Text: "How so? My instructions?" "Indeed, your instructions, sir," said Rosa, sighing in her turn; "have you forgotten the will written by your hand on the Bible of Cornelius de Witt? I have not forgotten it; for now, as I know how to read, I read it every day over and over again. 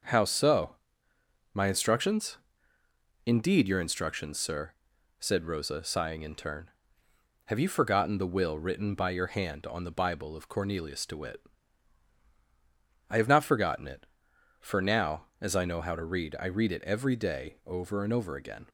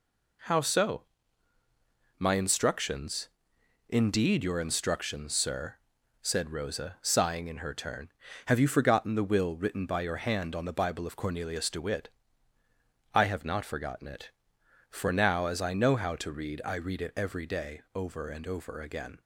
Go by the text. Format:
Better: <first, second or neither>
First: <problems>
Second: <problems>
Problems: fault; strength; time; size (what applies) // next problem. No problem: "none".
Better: second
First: skips "her"; at 6.3 s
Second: none